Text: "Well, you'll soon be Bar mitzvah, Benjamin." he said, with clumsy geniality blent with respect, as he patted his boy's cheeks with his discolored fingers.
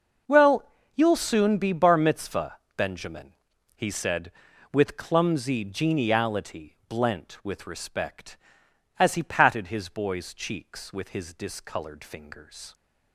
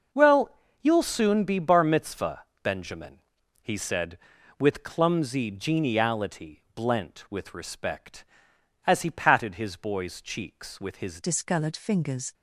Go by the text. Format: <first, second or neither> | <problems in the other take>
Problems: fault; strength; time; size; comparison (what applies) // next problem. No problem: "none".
first | changes voice at "discolored"; from 11.2 s on; 1.1 s long